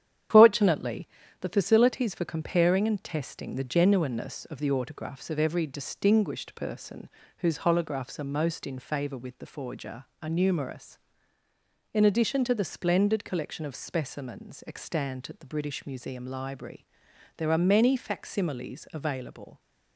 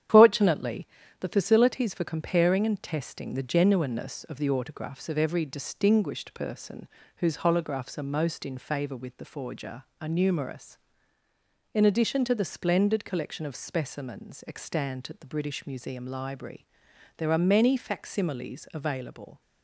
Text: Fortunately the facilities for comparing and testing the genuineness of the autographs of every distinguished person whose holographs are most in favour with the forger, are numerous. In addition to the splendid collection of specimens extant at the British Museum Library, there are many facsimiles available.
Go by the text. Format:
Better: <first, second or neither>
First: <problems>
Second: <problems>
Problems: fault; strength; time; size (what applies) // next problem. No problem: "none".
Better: neither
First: starts louder than the rest; strong; until 1.6 s; 9.5 dB // pauses between "Fortunately" and "the"; slight; at 1.0 s; 0.32 s long // pauses between "person" and "whose"; slight; at 7.0 s; 0.30 s long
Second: starts louder than the rest; strong; until 1.4 s; 9.5 dB // pauses between "Fortunately" and "the"; slight; at 0.8 s; 0.32 s long // pauses between "person" and "whose"; slight; at 6.8 s; 0.30 s long